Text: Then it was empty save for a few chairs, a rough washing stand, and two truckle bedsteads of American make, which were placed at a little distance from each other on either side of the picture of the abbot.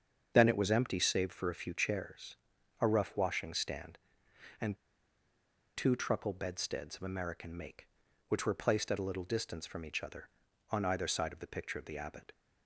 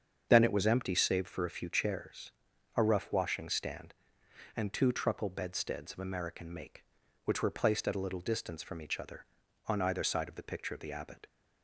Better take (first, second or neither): second